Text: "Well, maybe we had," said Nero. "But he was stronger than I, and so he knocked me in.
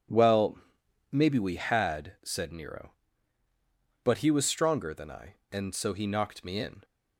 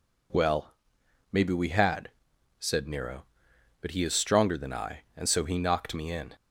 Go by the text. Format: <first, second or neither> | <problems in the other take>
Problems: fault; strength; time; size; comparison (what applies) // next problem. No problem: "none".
first | says "is" for "was"; at 4.0 s